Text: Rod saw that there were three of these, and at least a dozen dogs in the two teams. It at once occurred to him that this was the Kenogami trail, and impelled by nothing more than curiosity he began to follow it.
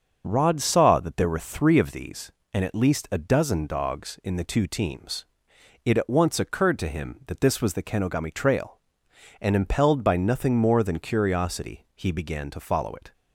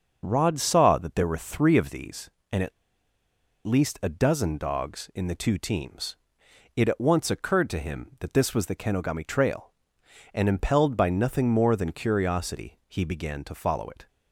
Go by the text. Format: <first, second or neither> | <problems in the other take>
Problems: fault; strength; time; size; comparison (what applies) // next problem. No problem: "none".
first | starts louder than the rest; until 1.2 s; 6.5 dB; also in the first // pauses between "at" and "least"; noticeable; at 2.7 s; 0.92 s long